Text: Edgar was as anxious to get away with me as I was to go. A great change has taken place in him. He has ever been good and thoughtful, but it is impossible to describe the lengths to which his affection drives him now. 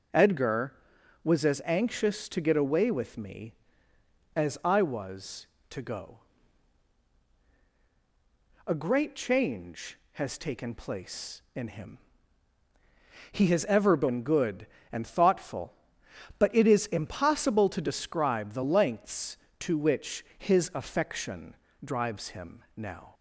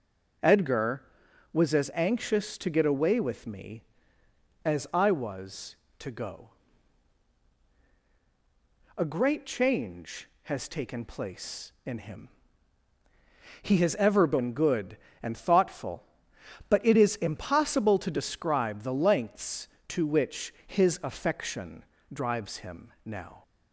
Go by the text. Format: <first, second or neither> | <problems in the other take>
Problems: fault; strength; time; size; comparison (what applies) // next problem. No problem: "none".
neither | pauses between "affection" and "drives"; slight; the same in both